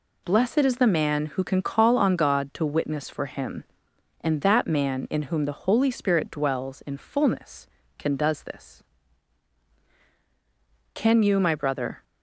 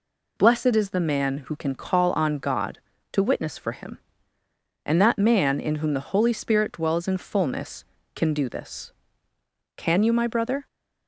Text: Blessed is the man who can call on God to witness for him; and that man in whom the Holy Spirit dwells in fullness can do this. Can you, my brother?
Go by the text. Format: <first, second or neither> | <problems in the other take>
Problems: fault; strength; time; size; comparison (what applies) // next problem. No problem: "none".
second | says "does" for "do"; at 8.1 s